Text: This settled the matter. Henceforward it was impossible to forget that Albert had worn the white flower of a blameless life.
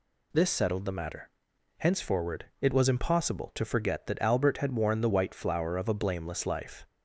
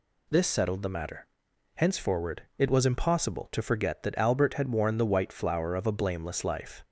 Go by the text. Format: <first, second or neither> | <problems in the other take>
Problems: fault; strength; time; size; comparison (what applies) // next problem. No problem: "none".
neither | pauses between "Henceforward" and "it"; slight; the same in both